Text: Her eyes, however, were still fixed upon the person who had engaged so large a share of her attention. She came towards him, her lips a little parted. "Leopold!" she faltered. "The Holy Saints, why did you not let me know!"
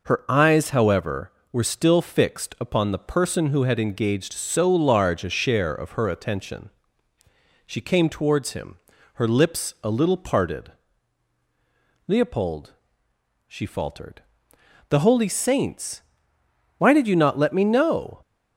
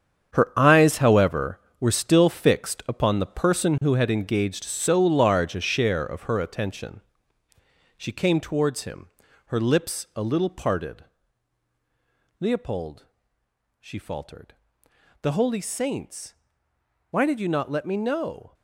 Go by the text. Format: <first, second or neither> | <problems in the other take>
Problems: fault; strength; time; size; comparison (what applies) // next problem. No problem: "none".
first | gets quieter; strong; throughout; 10 dB